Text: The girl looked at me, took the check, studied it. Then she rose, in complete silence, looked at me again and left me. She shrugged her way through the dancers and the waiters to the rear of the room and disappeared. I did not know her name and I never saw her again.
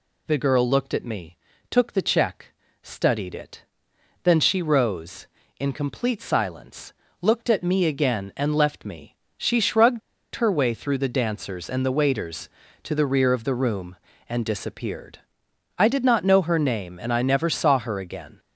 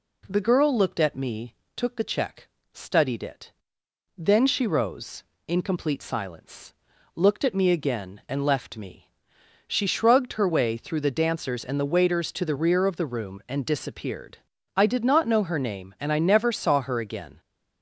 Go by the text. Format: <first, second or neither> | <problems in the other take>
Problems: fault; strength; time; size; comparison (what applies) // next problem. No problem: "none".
second | pauses between "shrugged" and "her"; slight; at 10.0 s; 0.35 s long